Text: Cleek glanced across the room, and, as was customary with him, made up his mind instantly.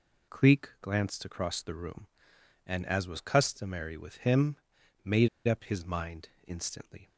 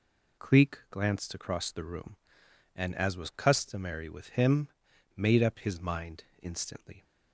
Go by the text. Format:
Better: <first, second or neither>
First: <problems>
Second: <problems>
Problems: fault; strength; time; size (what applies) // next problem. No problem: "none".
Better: second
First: pauses between "made" and "up"; slight; at 5.2 s; 0.19 s long // pauses between "mind" and "instantly"; slight; at 6.2 s; 0.18 s long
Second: pauses between "mind" and "instantly"; slight; at 6.2 s; 0.18 s long